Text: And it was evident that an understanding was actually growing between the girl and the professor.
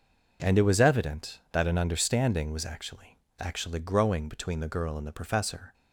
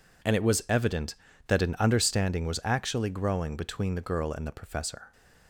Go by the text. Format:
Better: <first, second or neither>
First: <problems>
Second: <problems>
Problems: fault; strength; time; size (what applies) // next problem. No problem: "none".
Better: second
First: says "actually" twice; at 3.3 s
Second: none